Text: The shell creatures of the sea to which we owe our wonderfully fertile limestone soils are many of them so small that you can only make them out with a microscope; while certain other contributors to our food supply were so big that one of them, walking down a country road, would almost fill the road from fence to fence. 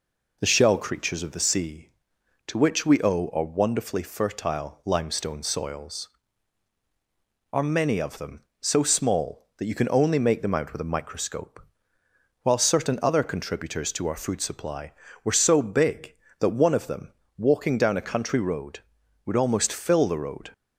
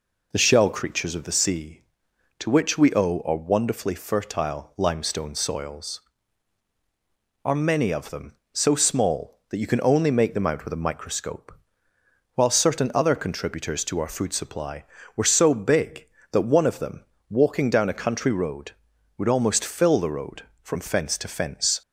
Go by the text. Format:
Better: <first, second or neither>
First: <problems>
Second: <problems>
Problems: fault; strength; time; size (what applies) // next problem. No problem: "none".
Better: second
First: stops before "from fence to fence"; at 20.5 s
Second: none